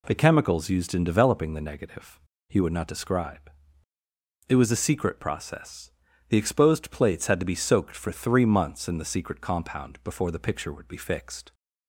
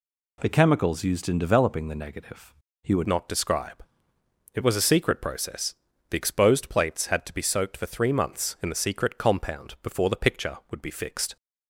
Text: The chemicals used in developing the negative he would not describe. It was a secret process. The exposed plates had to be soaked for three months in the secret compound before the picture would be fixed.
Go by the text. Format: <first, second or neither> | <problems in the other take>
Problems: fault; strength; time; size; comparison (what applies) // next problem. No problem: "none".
first | pauses between "negative" and "he"; slight; at 2.5 s; 0.30 s long; slight in the first // changes voice at "not"; from 3.0 s on; 8.3 s long